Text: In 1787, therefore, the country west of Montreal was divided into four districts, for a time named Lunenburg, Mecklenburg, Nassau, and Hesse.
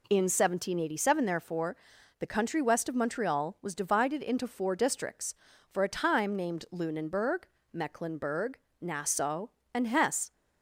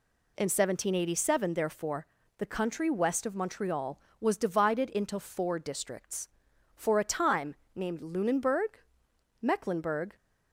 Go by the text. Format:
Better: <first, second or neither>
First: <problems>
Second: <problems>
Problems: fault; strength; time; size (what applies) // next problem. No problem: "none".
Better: first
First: none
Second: pauses between "time" and "named"; slight; at 7.5 s; 0.22 s long // stops before "Nassau and Hesse"; at 10.1 s